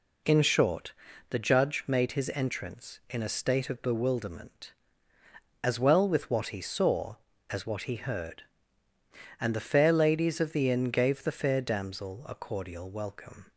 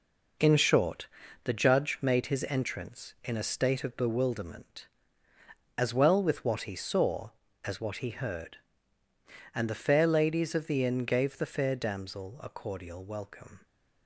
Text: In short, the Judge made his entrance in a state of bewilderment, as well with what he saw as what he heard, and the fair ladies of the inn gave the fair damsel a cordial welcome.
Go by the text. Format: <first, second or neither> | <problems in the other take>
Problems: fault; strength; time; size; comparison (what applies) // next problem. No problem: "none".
first | gets quieter; strong; throughout; 7.5 dB